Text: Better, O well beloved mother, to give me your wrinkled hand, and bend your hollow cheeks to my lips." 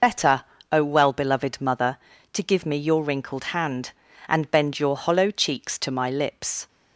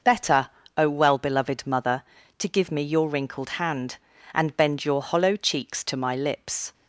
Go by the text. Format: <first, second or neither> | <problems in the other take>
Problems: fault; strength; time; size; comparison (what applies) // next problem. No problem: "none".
second | loses the start of "Better"; at 0.0 s; 50 ms